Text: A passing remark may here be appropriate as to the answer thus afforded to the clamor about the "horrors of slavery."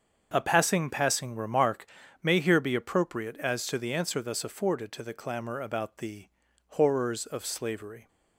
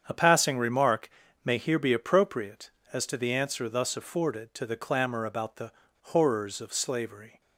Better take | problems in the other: second | starts louder than the rest; until 1.3 s; 7 dB; strong in the second // says "passing" twice; at 0.8 s // pauses between "remark" and "may"; at 1.8 s; 0.38 s long; slight in the second // pauses between "the" and "horrors"; at 6.2 s; 0.40 s long; slight in the second

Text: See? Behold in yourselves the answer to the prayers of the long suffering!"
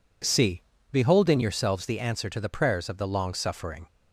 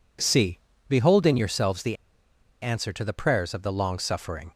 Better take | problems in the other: first | pauses between "the" and "answer"; noticeable; at 1.9 s; 0.66 s long

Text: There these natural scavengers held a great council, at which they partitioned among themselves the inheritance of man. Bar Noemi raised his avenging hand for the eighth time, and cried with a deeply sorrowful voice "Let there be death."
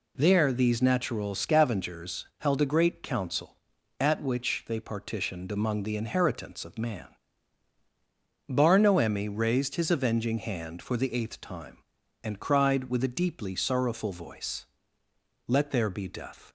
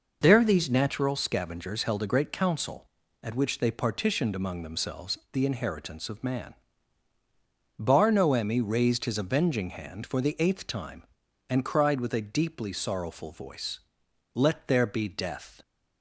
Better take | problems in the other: second | skips "themselves"; at 5.8 s // pauses between "voice" and "Let"; noticeable; at 14.6 s; 0.82 s long; noticeable in the second

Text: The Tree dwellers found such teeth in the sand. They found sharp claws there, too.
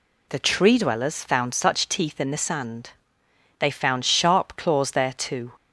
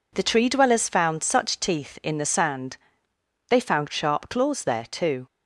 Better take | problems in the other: neither | none

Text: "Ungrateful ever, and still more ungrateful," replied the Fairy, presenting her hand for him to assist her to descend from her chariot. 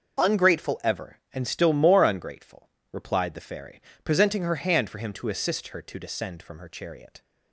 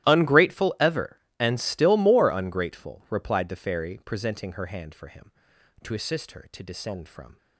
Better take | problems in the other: first | starts louder than the rest; strong; until 1.1 s; 15 dB // stops before "her chariot"; at 7.3 s

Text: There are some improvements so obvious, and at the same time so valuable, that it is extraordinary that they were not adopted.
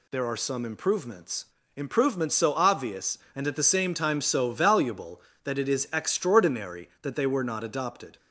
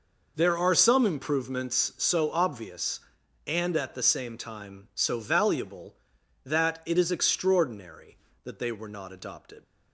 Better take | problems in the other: second | says "improvements" twice; at 1.7 s

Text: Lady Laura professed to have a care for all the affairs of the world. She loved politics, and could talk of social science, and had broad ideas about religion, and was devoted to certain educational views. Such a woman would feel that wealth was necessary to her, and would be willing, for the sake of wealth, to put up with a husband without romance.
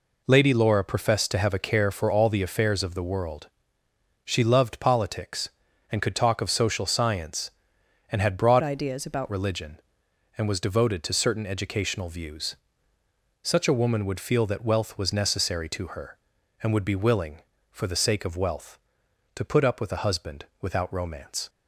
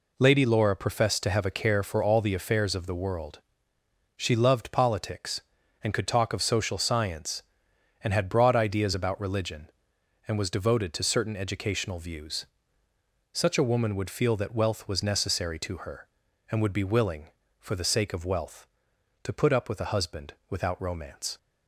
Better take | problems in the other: second | changes voice from "ideas" to "about"; from 8.6 to 9.2 s; 0.6 s long // pauses between "husband" and "without"; slight; at 20.4 s; 0.16 s long; slight in the second

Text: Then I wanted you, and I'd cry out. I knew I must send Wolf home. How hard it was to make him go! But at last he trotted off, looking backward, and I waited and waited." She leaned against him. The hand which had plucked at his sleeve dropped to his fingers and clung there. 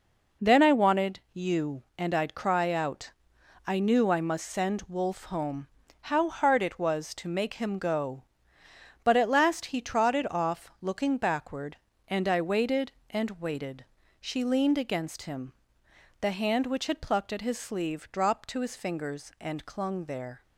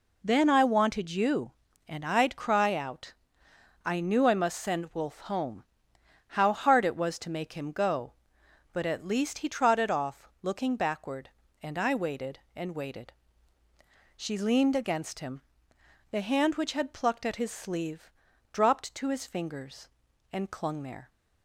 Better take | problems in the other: first | says "least" for "last"; at 9.0 s // pauses between "sleeve" and "dropped"; at 18.1 s; 0.40 s long

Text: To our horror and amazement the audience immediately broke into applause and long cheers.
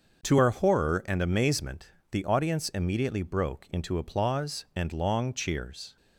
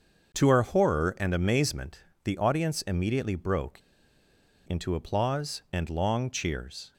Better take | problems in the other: first | starts louder than the rest; until 1.3 s; 6.5 dB; also in the first // pauses between "amazement" and "the"; slight; at 2.0 s; 0.20 s long; slight in the first // pauses between "broke" and "into"; noticeable; at 3.8 s; 0.86 s long

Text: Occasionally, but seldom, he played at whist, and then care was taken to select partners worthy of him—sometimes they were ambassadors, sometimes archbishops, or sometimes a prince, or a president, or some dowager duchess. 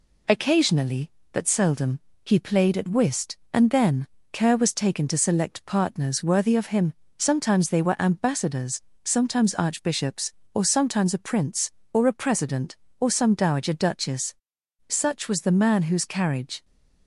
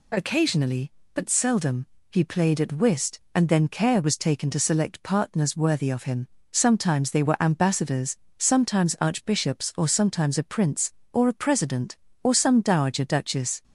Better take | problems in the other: second | pauses between "then" and "care"; slight; at 4.0 s; 0.26 s long // goes on to say "Such was the man whose carriage"; strong; from 14.8 s on; 1.7 s long

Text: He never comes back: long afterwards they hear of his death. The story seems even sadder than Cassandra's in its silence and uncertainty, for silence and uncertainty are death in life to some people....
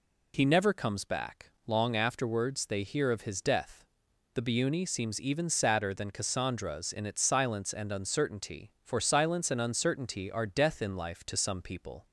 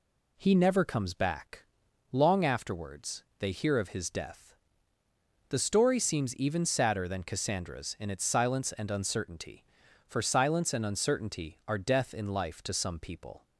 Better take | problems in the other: second | says "biuni" for "story"; at 4.4 s

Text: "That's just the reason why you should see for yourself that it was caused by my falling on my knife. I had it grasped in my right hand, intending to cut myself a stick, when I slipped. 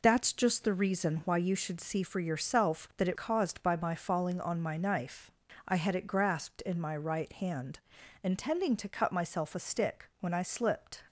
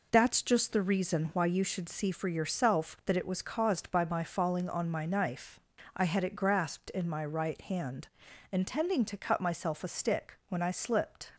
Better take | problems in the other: second | skips "was"; at 3.1 s

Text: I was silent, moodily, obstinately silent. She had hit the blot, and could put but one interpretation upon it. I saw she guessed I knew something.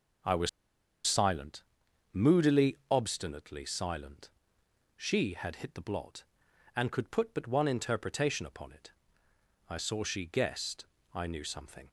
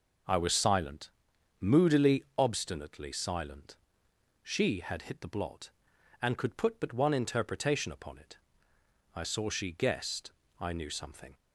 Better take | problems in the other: second | pauses between "was" and "silent"; noticeable; at 0.4 s; 0.57 s long // pauses between "guessed" and "I"; slight; at 10.8 s; 0.30 s long; slight in the second

